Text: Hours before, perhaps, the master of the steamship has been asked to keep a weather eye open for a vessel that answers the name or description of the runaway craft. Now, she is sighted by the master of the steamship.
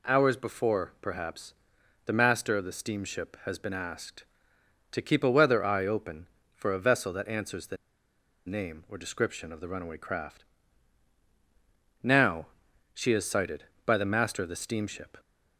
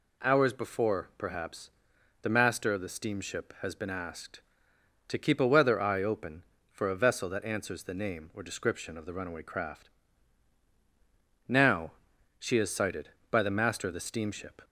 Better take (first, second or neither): second